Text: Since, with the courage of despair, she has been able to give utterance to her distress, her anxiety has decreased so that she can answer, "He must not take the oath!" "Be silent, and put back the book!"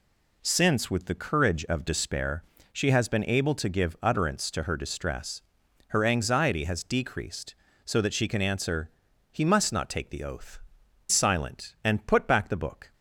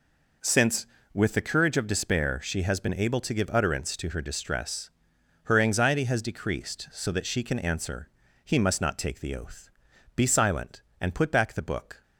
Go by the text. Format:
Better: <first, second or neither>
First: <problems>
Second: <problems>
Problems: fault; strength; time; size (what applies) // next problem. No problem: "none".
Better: second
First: skips "Be"; at 10.8 s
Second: none